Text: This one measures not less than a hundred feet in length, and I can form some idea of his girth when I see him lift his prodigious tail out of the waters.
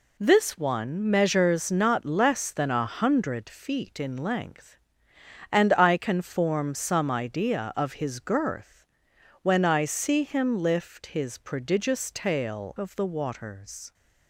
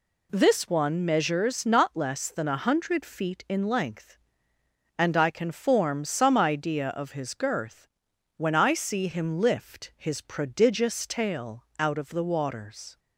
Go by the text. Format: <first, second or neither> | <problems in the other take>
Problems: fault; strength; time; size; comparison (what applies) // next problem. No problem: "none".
second | pauses between "girth" and "when"; noticeable; at 8.8 s; 0.56 s long; noticeable in the second // skips "out"; at 12.7 s